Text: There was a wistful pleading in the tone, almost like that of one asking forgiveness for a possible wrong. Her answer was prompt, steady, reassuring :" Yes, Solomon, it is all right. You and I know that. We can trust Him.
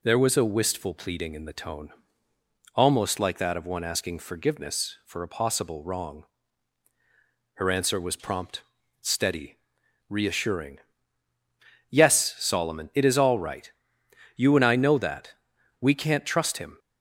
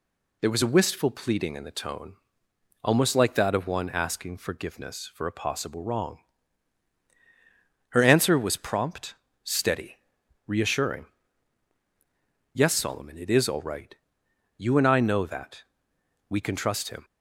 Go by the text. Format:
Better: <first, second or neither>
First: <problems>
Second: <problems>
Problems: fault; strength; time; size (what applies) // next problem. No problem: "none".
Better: second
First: says "can't" for "can"; at 15.9 s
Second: none